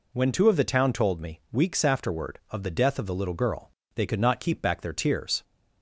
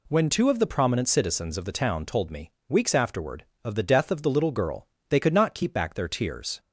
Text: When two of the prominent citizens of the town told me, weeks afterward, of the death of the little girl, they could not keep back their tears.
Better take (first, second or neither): second